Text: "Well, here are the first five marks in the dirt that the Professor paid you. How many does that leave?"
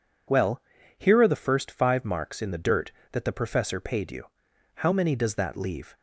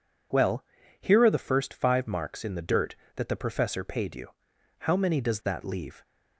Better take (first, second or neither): neither